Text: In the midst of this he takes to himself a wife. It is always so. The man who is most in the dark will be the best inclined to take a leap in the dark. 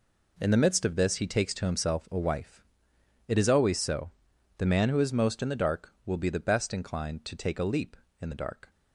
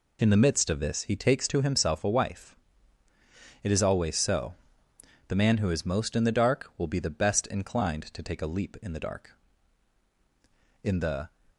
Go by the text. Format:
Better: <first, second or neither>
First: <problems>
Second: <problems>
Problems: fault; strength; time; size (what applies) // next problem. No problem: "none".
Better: first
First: none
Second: goes on to say "In the"; slight; from 10.8 s on; 0.46 s long